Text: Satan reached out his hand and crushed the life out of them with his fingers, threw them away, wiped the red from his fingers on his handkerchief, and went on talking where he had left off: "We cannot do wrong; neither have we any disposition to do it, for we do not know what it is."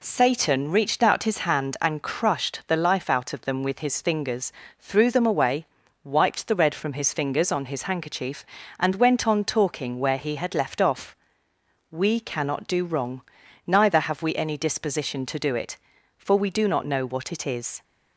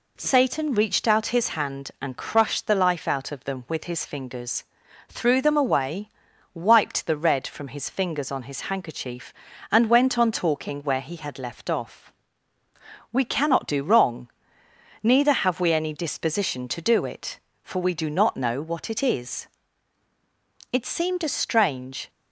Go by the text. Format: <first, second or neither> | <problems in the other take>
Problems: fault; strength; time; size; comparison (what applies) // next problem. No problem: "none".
first | goes on to say "It seemed a strange"; from 20.7 s on; 1.3 s long